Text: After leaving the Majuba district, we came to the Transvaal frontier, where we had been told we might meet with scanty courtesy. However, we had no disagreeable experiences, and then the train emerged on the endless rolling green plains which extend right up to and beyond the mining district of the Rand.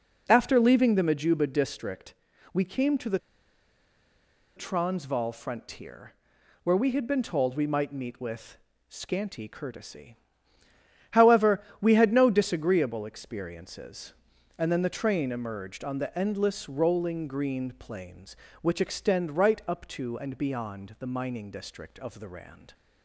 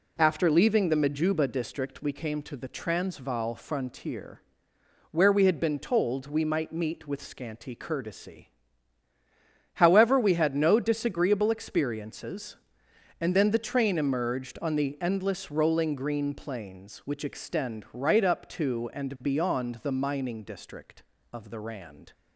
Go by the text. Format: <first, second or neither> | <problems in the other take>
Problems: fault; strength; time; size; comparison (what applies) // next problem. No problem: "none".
second | pauses between "the" and "Transvaal"; strong; at 3.1 s; 1.3 s long // pauses between "with" and "scanty"; slight; at 8.5 s; 0.32 s long